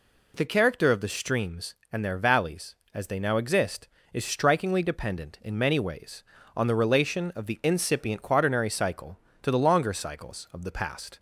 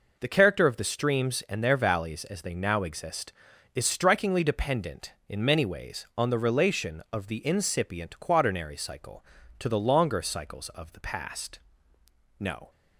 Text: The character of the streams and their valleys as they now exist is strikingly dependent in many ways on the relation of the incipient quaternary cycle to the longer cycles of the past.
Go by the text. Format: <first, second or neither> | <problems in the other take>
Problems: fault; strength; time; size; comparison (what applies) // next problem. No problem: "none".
first | goes on to say "No"; slight; from 12.3 s on; 0.30 s long